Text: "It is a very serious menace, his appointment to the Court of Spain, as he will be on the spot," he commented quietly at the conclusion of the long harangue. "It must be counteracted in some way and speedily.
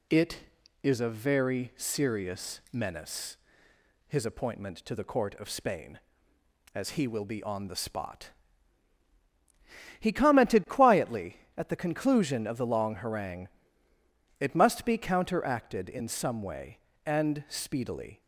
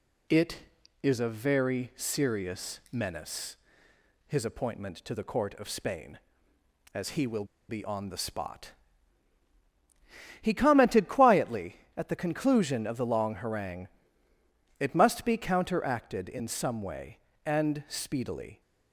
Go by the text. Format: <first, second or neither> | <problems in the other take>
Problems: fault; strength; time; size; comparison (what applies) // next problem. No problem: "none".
first | pauses between "will" and "be"; slight; at 7.4 s; 0.25 s long